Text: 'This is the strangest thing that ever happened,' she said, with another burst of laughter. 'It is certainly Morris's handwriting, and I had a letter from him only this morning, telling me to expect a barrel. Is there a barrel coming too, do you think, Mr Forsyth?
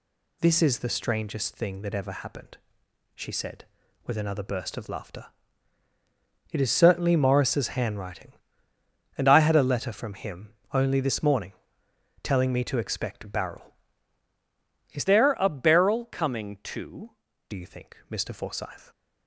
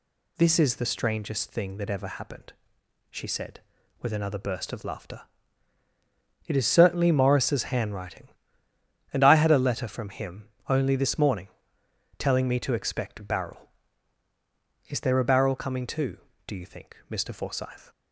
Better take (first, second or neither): second